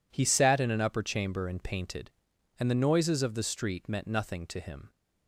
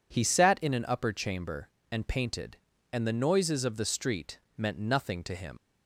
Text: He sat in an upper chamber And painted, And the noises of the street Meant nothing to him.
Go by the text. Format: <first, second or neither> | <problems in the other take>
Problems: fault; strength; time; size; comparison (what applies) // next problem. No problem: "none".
first | pauses between "street" and "Meant"; slight; at 4.3 s; 0.18 s long // leaves "him" unfinished; at 5.5 s; 70 ms